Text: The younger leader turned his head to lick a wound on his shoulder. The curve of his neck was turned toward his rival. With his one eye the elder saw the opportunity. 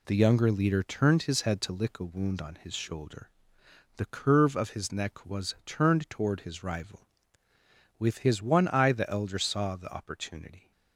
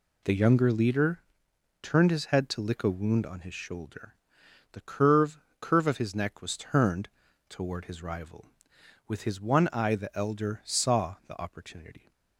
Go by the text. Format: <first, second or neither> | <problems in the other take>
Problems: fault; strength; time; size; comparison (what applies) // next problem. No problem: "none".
first | pauses between "leader" and "turned"; noticeable; at 1.2 s; 0.58 s long // says "curve" twice; at 5.6 s // pauses between "turned" and "toward"; at 7.0 s; 0.40 s long